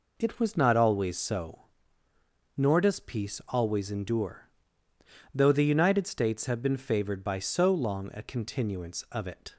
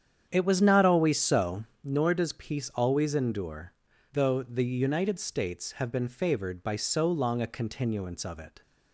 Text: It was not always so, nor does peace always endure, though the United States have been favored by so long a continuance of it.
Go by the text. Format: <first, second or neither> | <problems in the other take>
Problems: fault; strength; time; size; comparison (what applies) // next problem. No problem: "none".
first | starts louder than the rest; strong; until 1.9 s; 8.5 dB